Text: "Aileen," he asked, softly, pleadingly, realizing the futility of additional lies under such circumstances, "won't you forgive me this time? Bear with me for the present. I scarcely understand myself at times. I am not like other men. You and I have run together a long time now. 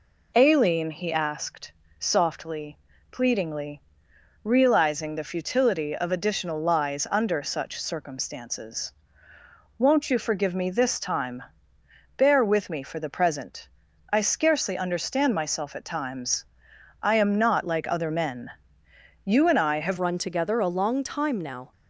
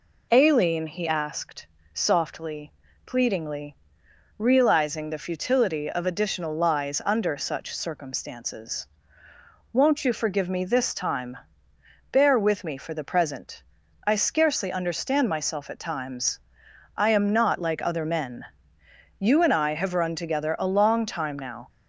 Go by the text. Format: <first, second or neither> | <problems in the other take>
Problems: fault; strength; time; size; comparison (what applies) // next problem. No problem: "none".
second | changes voice at "run"; from 19.9 s on; 1.8 s long